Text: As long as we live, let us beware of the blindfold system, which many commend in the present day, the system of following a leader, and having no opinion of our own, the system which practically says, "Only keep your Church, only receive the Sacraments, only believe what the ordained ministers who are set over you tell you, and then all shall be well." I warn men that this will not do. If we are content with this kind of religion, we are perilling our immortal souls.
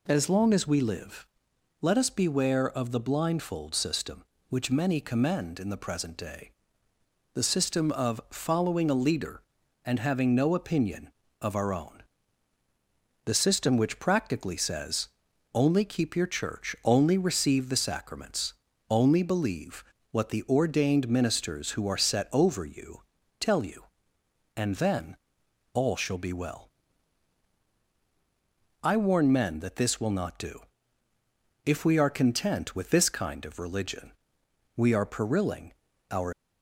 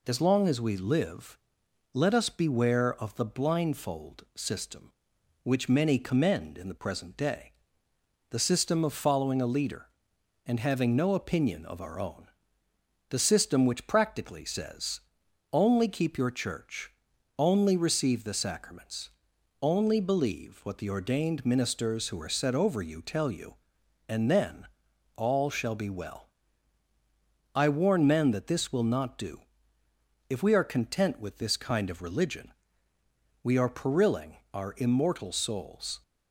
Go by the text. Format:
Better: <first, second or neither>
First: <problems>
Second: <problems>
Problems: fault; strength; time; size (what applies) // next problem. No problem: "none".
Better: second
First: pauses between "believe" and "what"; slight; at 19.8 s; 0.30 s long // pauses between "you" and "tell"; at 23.0 s; 0.38 s long // pauses between "then" and "all"; noticeable; at 25.1 s; 0.56 s long // pauses between "perilling" and "our"; at 35.7 s; 0.40 s long // stops before "immortal souls"; at 36.3 s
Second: pauses between "then" and "all"; noticeable; at 24.6 s; 0.50 s long // pauses between "perilling" and "our"; slight; at 34.3 s; 0.16 s long